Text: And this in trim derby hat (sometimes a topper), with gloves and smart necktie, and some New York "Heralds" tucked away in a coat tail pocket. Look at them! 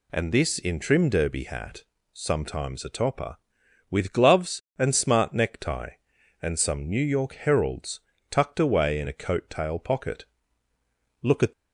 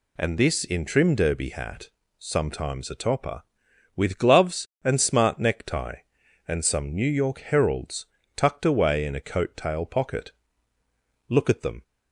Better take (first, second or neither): second